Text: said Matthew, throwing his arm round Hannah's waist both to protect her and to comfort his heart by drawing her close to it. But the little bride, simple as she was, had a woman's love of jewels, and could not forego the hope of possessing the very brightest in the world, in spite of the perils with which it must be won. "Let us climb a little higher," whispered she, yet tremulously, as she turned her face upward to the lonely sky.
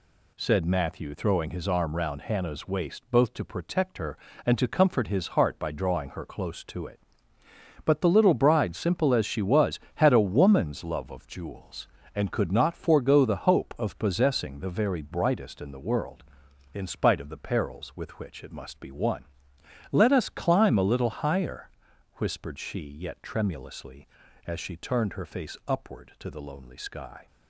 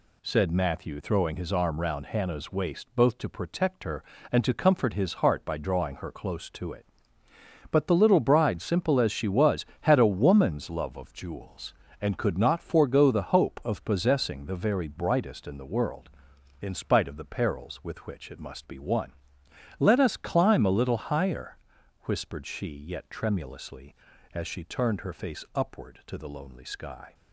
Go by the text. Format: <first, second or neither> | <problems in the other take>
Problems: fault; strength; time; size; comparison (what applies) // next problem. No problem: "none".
neither | none